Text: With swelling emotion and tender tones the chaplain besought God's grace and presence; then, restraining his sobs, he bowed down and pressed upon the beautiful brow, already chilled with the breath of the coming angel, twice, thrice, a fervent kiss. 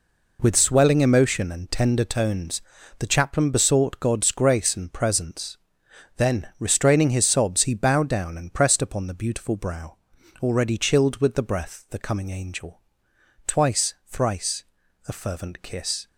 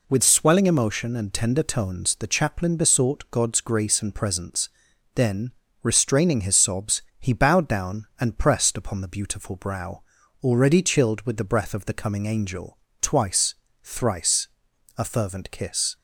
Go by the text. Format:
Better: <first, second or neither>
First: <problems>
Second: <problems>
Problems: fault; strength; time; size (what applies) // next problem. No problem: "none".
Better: second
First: pauses between "tones" and "the"; slight; at 2.6 s; 0.34 s long // skips "of"; at 11.8 s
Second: none